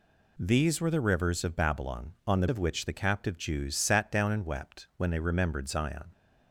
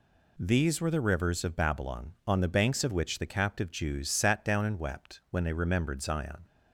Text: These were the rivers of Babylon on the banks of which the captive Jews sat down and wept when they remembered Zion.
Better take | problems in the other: second | skips "banks"; at 2.4 s

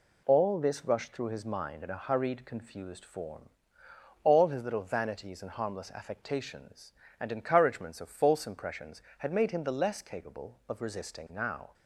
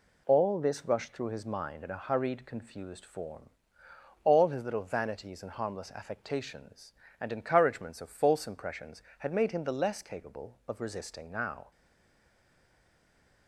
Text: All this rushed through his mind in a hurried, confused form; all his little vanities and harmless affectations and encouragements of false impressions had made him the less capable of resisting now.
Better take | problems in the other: first | stays silent after the last word; noticeable; from 11.7 s on; 1.7 s long

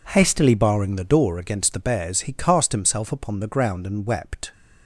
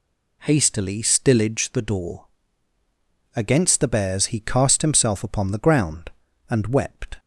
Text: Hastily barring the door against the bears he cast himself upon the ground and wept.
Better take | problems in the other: first | says "stillage" for "barring"; at 1.0 s // pauses between "door" and "against"; at 2.2 s; 1.1 s long

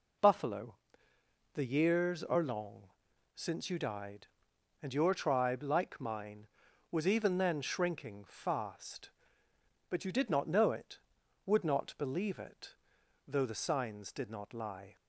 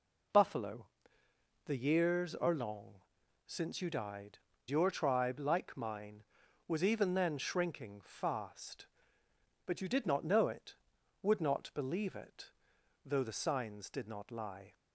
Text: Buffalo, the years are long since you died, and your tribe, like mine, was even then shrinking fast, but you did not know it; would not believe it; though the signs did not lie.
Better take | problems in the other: first | pauses between "long" and "since"; noticeable; at 2.9 s; 0.50 s long; noticeable in the first // skips "and"; at 4.5 s

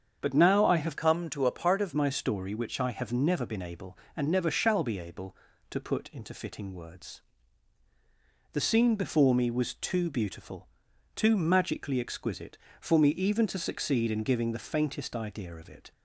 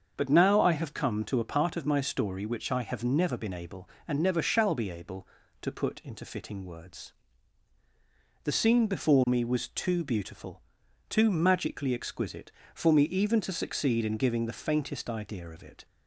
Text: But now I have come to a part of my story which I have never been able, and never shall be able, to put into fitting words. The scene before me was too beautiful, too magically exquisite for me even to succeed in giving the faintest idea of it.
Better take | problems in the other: second | starts louder than the rest; strong; until 1.2 s; 7.5 dB; also in the second // changes voice from "come" to "of"; from 0.9 to 1.9 s; 1.0 s long

